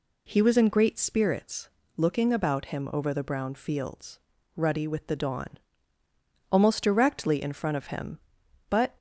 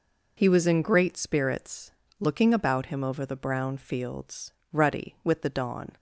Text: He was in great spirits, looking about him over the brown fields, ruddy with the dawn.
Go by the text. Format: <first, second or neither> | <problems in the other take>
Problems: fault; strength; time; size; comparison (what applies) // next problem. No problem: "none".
second | goes on to say "Almost directly in front of him but"; strong; from 6.5 s on; 2.4 s long